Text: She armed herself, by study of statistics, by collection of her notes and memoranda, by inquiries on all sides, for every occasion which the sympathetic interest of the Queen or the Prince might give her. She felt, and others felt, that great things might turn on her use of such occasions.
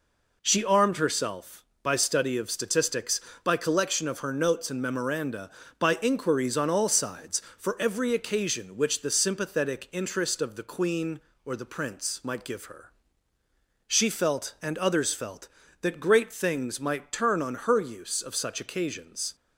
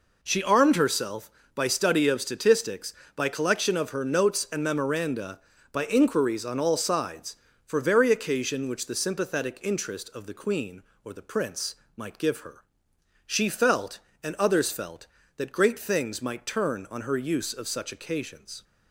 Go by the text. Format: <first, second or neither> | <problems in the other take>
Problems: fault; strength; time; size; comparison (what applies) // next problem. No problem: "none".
first | says "very" for "every"; at 7.7 s // pauses between "Prince" and "might"; slight; at 11.7 s; 0.22 s long